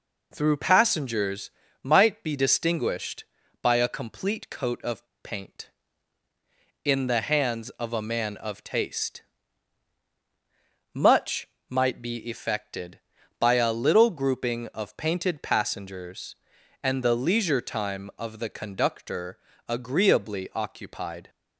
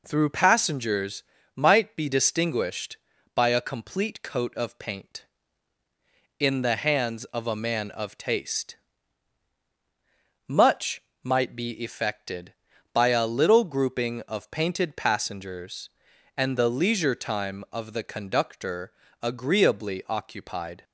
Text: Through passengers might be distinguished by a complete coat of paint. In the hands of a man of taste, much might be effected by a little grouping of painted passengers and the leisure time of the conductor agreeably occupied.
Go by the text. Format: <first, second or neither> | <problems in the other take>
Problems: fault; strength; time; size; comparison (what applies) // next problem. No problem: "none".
second | pauses between "passengers" and "might"; slight; at 1.5 s; 0.32 s long; slight in the second // pauses between "of" and "paint"; slight; at 5.0 s; 0.19 s long // pauses between "much" and "might"; slight; at 11.4 s; 0.22 s long; slight in the second // pauses between "conductor" and "agreeably"; slight; at 19.3 s; 0.30 s long; slight in the second